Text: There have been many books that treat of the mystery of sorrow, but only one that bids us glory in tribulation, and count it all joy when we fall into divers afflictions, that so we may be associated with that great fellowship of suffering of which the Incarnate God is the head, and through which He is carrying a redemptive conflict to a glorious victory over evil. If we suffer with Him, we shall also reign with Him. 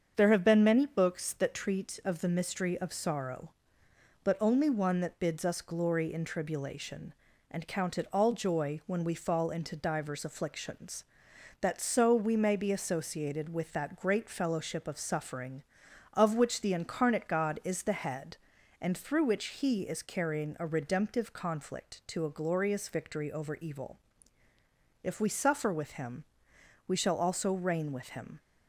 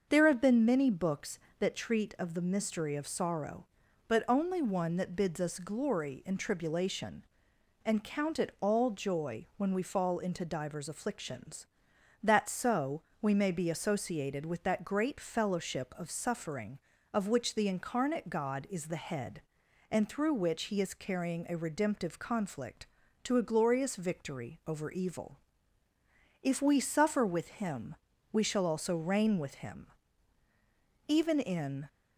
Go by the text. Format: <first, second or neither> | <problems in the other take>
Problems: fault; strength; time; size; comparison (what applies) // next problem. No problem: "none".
first | starts louder than the rest; until 1.1 s; 6.5 dB; also in the first // pauses between "so" and "we"; slight; at 13.0 s; 0.18 s long // goes on to say "Even in"; noticeable; from 31.0 s on; 0.80 s long